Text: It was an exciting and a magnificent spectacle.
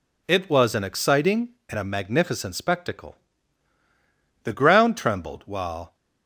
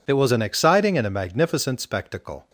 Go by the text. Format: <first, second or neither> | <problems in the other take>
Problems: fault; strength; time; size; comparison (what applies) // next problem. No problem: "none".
second | goes on to say "The ground trembled while"; from 4.4 s on; 1.5 s long